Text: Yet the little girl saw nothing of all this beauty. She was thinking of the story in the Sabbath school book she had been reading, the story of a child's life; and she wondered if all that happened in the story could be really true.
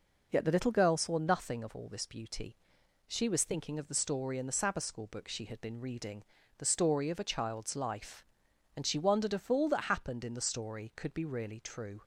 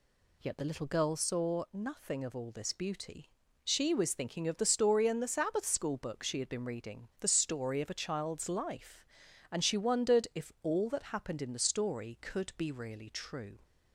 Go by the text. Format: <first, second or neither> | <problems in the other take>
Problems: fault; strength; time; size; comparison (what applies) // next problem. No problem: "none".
neither | none